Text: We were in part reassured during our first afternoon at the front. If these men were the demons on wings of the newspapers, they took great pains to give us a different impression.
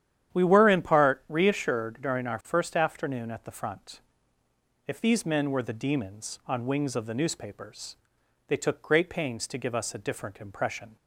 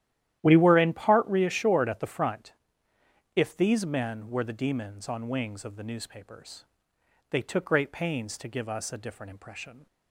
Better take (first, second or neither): first